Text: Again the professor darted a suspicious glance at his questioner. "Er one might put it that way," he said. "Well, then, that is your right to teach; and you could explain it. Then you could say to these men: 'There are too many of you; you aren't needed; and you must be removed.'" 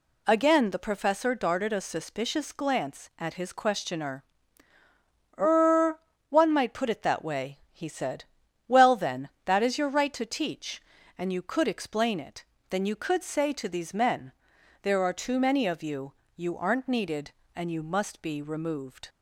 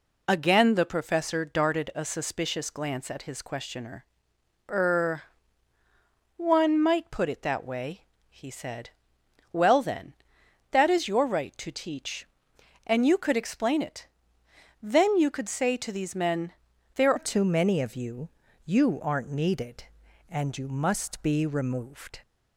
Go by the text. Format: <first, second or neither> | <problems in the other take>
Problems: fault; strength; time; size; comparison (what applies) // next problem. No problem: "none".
first | pauses between "Er" and "one"; at 5.2 s; 1.1 s long; slight in the first // changes voice at "are"; from 17.1 s on; 5.1 s long